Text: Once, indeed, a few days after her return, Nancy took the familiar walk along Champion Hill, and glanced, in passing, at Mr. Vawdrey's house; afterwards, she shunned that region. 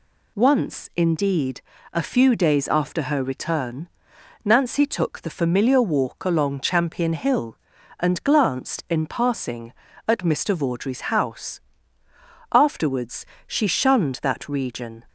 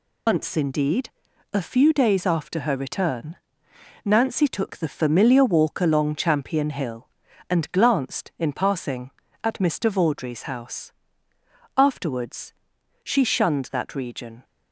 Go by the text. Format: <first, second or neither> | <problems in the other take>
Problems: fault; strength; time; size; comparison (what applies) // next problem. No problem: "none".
first | loses the start of "Once"; at 0.2 s; 95 ms